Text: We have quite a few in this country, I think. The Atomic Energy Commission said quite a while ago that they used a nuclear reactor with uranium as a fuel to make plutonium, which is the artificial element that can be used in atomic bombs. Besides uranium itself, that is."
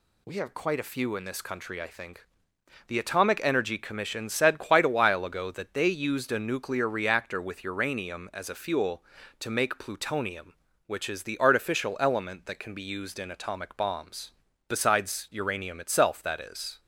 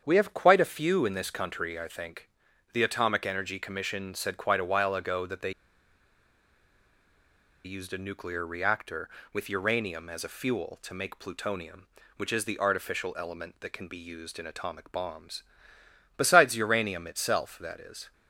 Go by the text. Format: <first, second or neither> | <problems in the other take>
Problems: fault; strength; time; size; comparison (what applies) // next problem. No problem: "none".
first | starts louder than the rest; strong; until 1.0 s; 7.5 dB // pauses between "they" and "used"; strong; at 5.5 s; 2.1 s long